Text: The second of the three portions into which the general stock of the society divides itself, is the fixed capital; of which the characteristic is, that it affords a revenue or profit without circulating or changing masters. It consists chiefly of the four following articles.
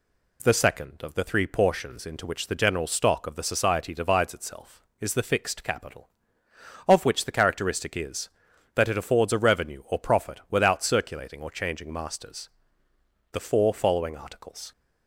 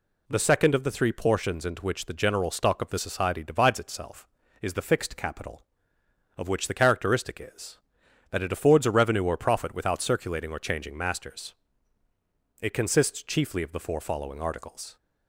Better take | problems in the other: second | skips "It consists chiefly of"; at 12.9 s

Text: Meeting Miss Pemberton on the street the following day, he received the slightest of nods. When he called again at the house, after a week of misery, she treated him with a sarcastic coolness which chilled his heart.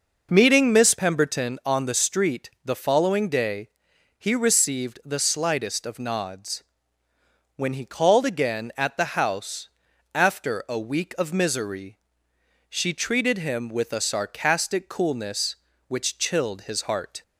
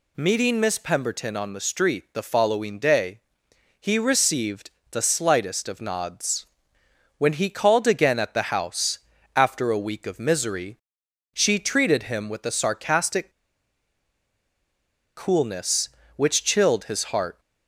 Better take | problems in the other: first | pauses between "received" and "the"; slight; at 4.7 s; 0.20 s long // pauses between "sarcastic" and "coolness"; strong; at 13.2 s; 1.8 s long

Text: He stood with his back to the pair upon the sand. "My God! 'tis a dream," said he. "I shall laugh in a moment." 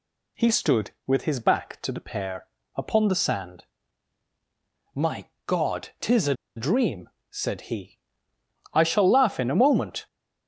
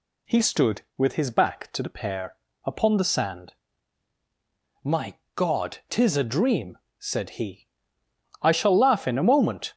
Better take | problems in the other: second | pauses between "pair" and "upon"; slight; at 2.4 s; 0.30 s long; slight in the second // pauses between "My" and "God"; slight; at 5.2 s; 0.16 s long; slight in the second // pauses between "a" and "dream"; slight; at 6.3 s; 0.22 s long

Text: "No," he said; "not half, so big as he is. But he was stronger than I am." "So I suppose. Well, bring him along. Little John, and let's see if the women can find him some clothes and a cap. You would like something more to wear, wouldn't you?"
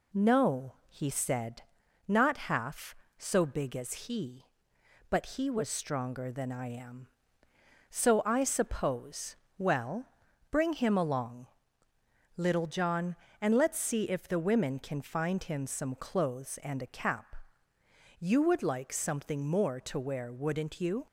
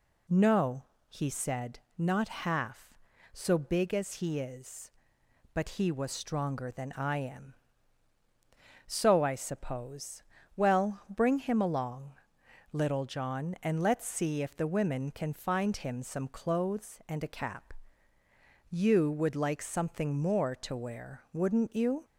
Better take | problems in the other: second | skips "is"; at 4.7 s

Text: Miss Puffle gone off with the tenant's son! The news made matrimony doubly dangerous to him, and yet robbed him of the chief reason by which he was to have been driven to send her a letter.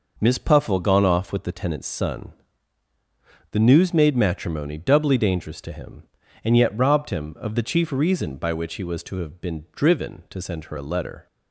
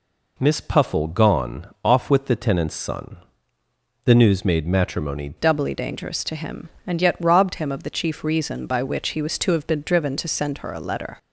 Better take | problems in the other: first | changes voice at "doubly"; from 5.3 s on; 5.8 s long

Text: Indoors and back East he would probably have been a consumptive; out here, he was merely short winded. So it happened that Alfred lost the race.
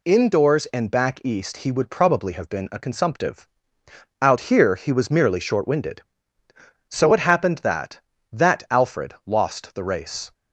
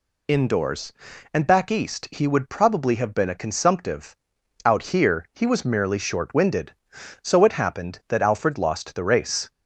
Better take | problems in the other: second | says "that" twice; at 8.3 s

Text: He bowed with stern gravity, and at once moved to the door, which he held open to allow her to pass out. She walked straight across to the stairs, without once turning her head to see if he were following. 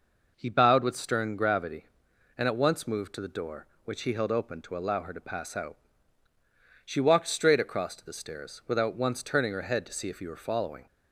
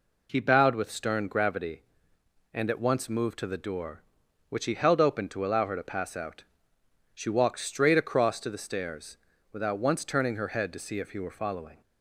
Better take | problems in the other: neither | none

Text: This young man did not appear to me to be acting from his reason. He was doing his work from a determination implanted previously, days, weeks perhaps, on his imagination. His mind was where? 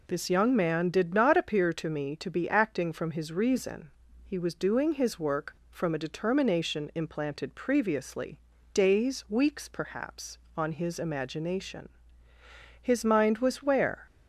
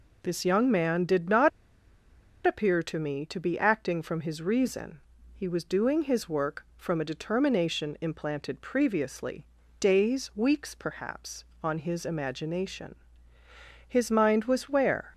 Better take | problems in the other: first | pauses between "not" and "appear"; noticeable; at 1.4 s; 0.96 s long

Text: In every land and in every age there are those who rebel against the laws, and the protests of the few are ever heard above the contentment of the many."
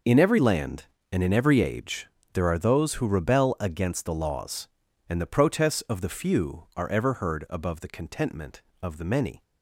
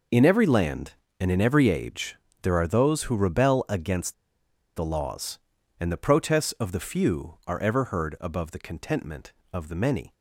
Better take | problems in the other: first | pauses between "age" and "there"; slight; at 2.1 s; 0.28 s long; slight in the first // pauses between "against" and "the"; noticeable; at 4.1 s; 0.63 s long

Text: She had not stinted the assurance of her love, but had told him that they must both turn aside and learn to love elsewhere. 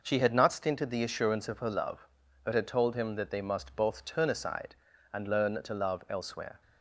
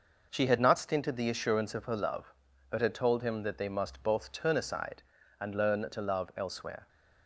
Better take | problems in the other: neither | none

